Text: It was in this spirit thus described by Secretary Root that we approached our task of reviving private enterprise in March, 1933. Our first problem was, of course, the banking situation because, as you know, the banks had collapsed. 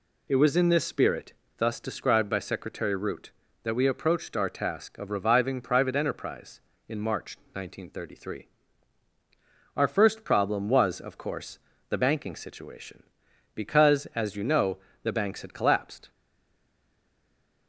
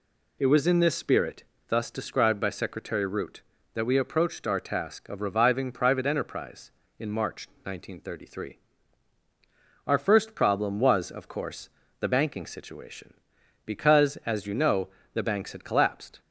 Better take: second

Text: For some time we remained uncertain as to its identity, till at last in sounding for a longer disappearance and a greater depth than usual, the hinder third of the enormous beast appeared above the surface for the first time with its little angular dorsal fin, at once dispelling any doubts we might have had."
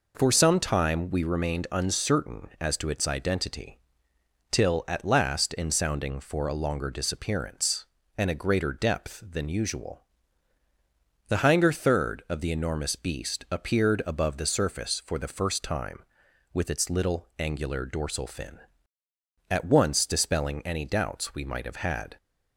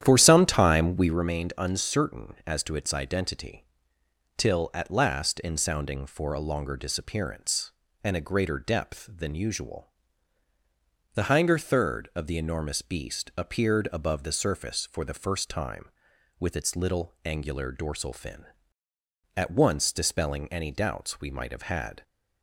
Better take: first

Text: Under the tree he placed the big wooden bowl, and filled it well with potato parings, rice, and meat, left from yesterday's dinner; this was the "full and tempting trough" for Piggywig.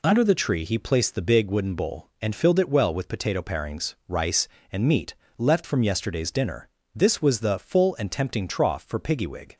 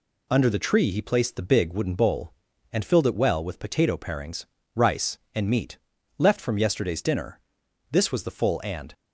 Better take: first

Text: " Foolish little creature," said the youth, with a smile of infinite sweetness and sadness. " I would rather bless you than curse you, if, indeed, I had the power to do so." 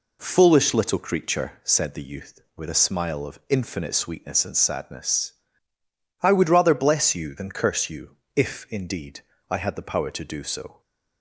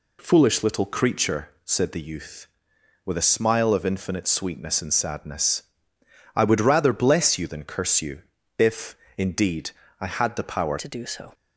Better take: first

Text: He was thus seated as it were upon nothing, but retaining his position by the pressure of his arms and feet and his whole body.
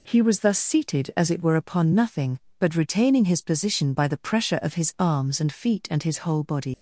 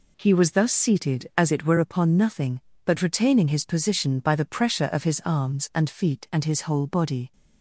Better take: second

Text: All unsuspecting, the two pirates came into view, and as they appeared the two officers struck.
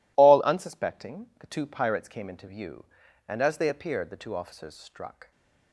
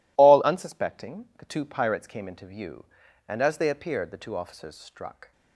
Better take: neither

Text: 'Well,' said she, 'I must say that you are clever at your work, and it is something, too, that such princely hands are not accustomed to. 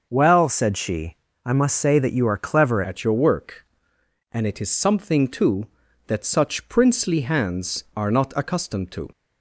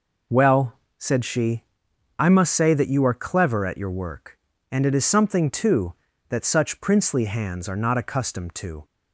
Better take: second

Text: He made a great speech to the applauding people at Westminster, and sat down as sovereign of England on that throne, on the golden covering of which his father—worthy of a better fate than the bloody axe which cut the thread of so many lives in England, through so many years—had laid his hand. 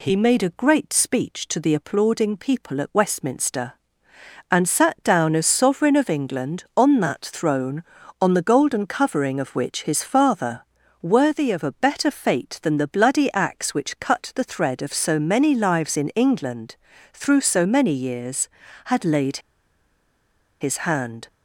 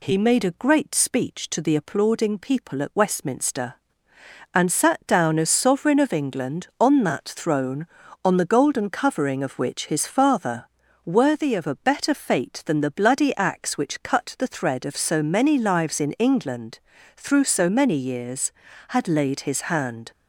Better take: second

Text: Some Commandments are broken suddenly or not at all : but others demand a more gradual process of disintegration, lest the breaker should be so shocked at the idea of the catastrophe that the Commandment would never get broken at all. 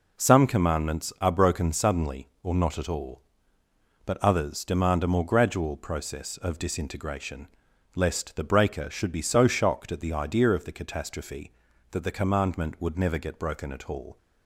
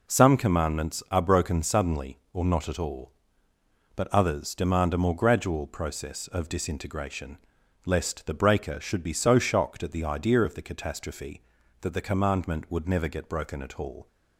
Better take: neither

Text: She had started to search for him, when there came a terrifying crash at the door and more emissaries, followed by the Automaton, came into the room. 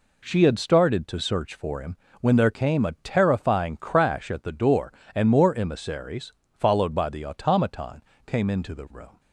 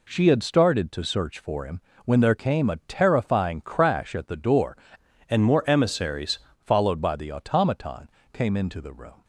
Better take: first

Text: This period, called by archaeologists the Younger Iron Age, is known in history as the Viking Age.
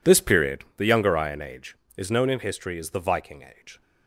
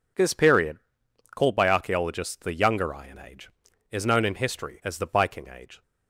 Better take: second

